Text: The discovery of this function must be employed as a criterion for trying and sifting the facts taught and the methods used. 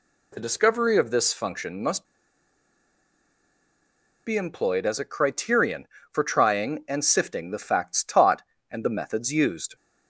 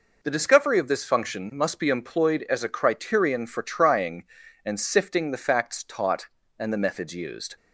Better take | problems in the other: second | pauses between "must" and "be"; strong; at 2.0 s; 2.1 s long

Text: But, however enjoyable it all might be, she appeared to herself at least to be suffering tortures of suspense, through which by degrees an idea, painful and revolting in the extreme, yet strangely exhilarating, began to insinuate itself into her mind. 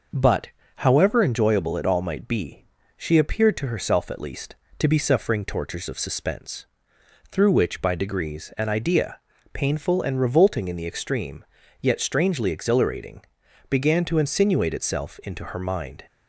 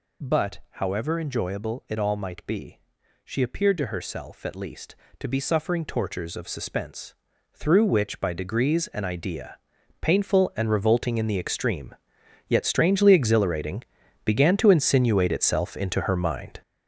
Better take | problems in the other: first | gets louder; strong; throughout; 8.5 dB

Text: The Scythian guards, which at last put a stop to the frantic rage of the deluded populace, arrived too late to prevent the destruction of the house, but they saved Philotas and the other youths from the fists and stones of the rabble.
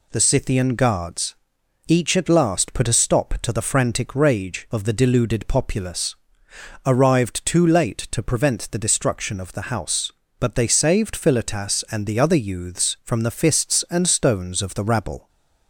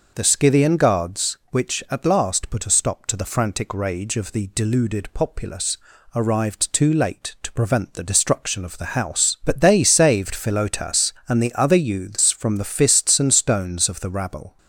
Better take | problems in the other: second | says "each" for "which"; at 1.8 s

